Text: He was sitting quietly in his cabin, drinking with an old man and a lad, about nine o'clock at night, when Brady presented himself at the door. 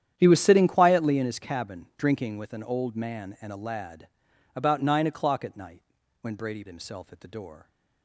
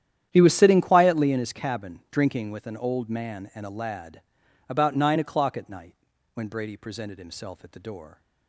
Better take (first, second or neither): second